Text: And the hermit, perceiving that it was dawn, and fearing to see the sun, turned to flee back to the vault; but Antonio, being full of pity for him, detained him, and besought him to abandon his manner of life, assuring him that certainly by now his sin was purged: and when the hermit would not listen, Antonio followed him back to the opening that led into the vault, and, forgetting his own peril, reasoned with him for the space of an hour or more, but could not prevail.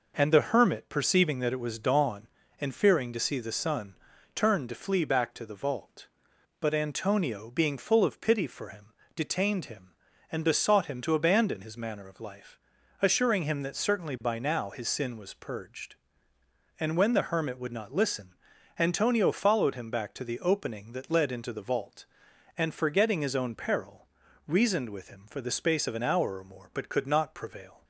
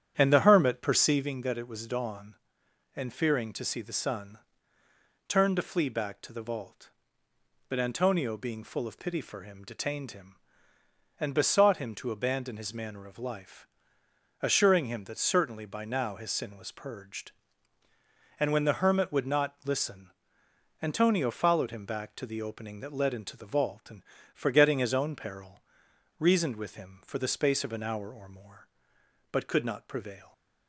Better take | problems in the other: first | starts louder than the rest; strong; until 1.4 s; 9.5 dB

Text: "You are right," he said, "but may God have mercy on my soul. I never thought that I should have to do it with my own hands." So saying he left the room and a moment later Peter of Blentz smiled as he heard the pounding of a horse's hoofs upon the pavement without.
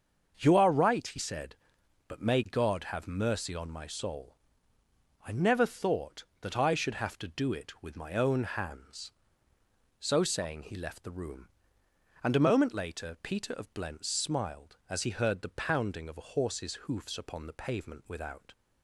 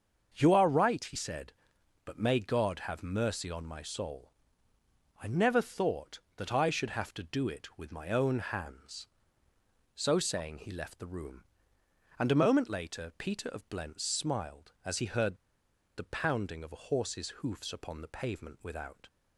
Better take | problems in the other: first | starts louder than the rest; until 1.3 s; 6.5 dB; also in the first // pauses between "heard" and "the"; noticeable; at 15.3 s; 0.61 s long

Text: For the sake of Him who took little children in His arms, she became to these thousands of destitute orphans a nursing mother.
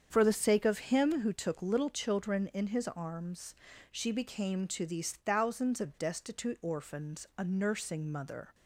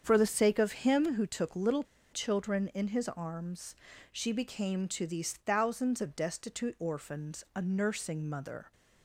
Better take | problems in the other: first | starts louder than the rest; strong; until 1.0 s; 7.5 dB; strong in the first // pauses between "little" and "children"; slight; at 1.8 s; 0.29 s long

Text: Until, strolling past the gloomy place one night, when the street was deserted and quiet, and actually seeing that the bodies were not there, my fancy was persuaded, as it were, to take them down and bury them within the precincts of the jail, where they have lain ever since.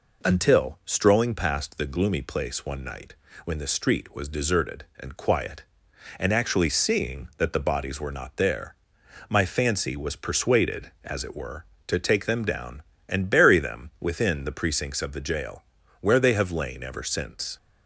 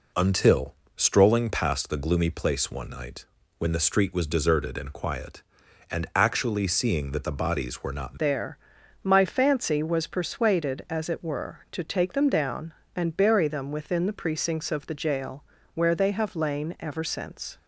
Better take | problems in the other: first | changes voice at "there"; from 8.1 s on; 9.4 s long

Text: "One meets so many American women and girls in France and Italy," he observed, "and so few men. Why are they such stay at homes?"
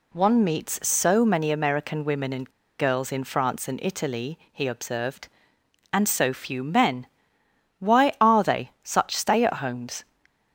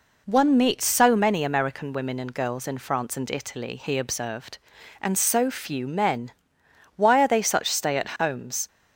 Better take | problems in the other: second | pauses between "and" and "girls"; slight; at 2.4 s; 0.29 s long

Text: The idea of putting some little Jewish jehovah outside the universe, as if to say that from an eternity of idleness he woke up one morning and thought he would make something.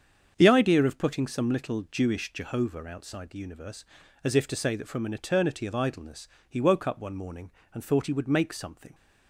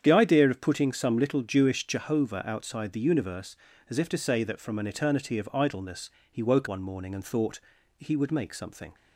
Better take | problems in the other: first | starts louder than the rest; strong; until 1.0 s; 8 dB; strong in the first // pauses between "idleness" and "he"; slight; at 6.0 s; 0.22 s long; slight in the first // skips "up"; at 6.6 s // pauses between "thought" and "he"; slight; at 7.6 s; 0.36 s long

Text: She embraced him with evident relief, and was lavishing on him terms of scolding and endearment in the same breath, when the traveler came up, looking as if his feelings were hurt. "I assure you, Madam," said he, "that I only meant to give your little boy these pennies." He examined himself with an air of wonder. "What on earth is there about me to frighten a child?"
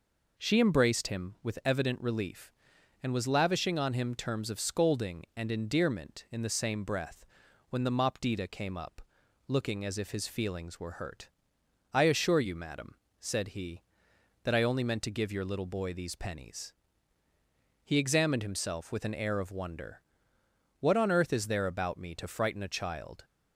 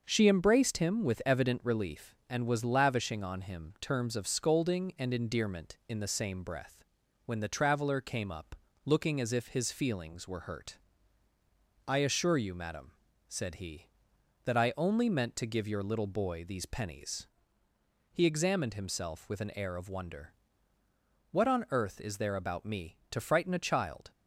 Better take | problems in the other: second | says "mopdita" for "traveler"; at 7.9 s

